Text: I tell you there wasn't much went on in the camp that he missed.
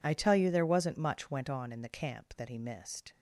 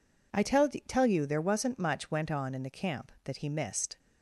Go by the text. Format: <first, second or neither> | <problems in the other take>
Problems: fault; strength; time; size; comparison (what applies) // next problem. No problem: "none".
first | says "tell" twice; at 0.8 s